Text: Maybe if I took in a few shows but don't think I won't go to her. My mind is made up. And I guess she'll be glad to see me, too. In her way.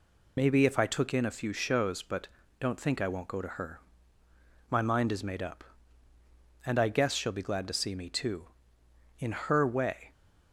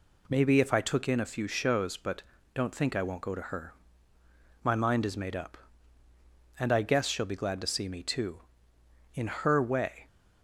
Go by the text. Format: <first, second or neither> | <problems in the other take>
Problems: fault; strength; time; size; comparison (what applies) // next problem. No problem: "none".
second | loses the start of "Maybe"; at 0.3 s; 65 ms // pauses between "but" and "don't"; slight; at 2.2 s; 0.32 s long; slight in the second